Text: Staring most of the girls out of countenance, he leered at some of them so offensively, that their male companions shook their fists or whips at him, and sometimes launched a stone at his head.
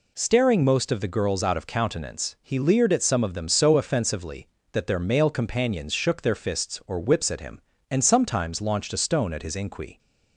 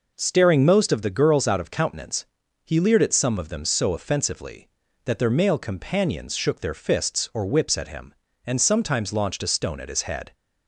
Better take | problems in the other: second | says "inqui" for "head"; at 9.5 s

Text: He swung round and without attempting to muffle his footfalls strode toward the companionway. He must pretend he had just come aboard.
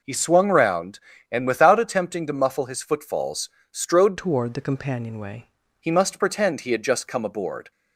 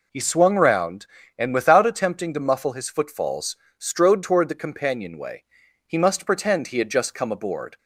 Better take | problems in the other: second | pauses between "footfalls" and "strode"; slight; at 3.4 s; 0.22 s long; slight in the second // changes voice from "toward" to "companionway"; from 4.1 to 5.4 s; 1.3 s long

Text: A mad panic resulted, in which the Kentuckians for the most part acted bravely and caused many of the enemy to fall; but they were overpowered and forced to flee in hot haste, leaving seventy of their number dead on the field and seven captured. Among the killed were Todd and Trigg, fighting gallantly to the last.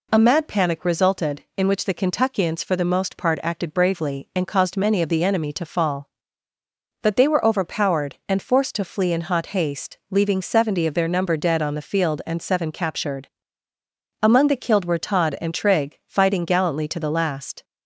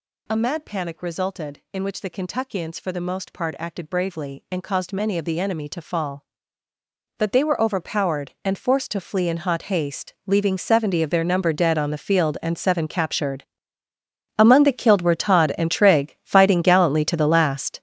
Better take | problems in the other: first | gets louder; strong; throughout; 11 dB

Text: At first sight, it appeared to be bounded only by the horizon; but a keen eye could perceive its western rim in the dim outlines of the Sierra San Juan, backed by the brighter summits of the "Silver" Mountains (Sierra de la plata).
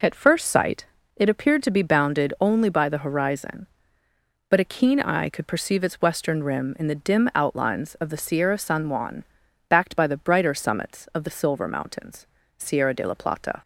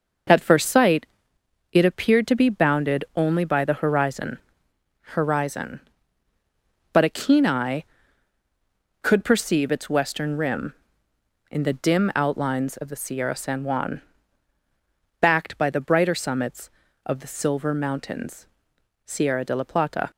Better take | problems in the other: first | starts louder than the rest; noticeable; until 1.9 s; 6 dB // says "horizon" twice; at 5.1 s

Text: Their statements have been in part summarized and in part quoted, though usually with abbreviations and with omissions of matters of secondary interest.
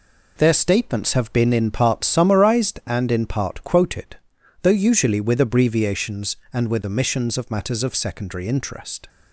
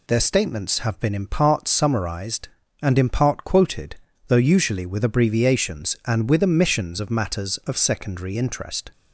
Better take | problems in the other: neither | none

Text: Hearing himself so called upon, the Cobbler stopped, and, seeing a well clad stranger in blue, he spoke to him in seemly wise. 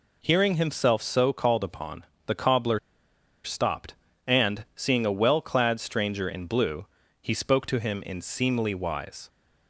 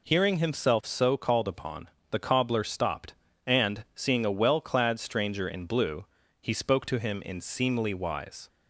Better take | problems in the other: second | pauses between "Cobbler" and "stopped"; noticeable; at 2.7 s; 0.66 s long

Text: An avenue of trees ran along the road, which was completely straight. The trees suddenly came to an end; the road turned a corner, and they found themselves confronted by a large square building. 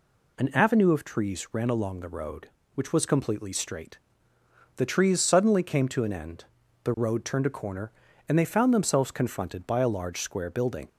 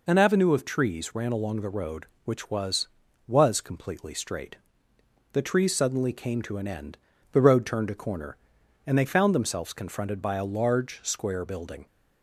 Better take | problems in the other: first | says "was" twice; at 3.2 s

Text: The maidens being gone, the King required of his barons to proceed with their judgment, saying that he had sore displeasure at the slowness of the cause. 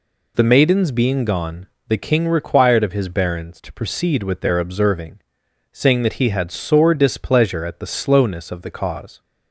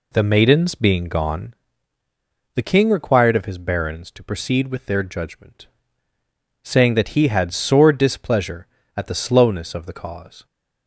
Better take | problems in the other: second | says "observing" for "judgment"; at 4.5 s

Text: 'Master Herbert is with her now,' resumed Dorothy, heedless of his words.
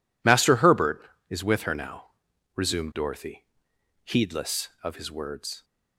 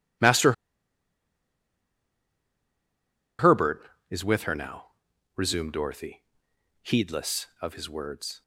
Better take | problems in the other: first | pauses between "Master" and "Herbert"; strong; at 0.5 s; 2.8 s long

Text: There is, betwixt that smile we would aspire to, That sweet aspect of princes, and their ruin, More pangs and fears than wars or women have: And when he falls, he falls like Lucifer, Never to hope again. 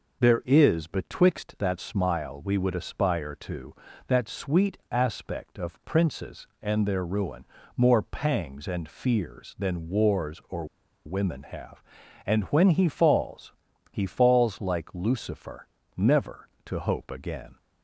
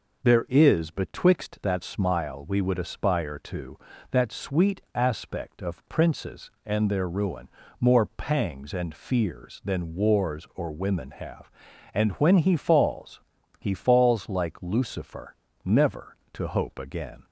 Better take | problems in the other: second | pauses between "or" and "women"; at 10.6 s; 0.40 s long

